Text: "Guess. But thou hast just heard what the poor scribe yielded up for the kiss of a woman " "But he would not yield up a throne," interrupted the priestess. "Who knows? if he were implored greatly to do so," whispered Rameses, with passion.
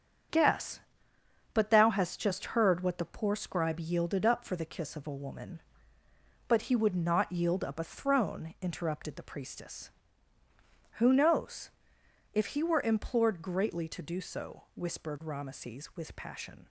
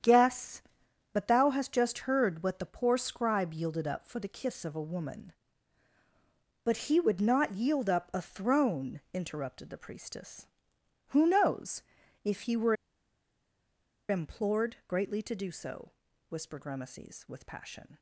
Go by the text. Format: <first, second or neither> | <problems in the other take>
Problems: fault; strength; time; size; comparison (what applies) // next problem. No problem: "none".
first | starts louder than the rest; strong; until 1.5 s; 9 dB; strong in the first // pauses between "were" and "implored"; strong; at 12.7 s; 1.3 s long